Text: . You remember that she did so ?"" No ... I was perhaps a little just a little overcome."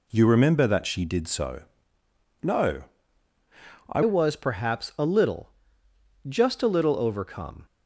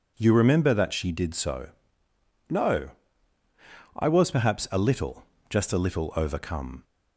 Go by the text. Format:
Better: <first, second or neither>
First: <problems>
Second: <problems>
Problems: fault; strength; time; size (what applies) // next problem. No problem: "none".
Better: second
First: changes voice at "was"; from 4.0 s on; 3.6 s long // pauses between "little" and "just"; noticeable; at 5.5 s; 0.74 s long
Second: pauses between "little" and "just"; slight; at 5.2 s; 0.24 s long